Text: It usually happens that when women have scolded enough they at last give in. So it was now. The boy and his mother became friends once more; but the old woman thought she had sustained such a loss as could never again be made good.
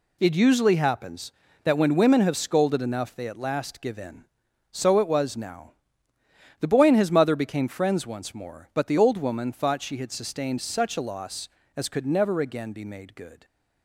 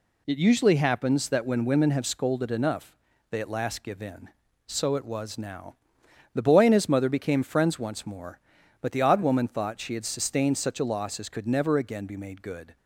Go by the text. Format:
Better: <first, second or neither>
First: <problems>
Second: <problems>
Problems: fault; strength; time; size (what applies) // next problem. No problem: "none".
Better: first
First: none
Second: pauses between "enough" and "they"; slight; at 2.9 s; 0.34 s long // says "odd" for "old"; at 9.0 s